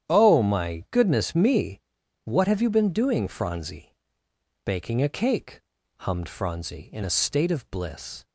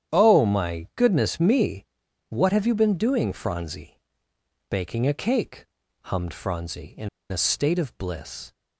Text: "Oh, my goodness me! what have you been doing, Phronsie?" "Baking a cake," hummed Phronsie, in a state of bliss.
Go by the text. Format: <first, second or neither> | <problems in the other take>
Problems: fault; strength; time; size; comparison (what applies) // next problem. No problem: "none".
first | starts louder than the rest; strong; until 1.2 s; 9.5 dB; strong in the first // pauses between "in" and "a"; slight; at 7.0 s; 0.23 s long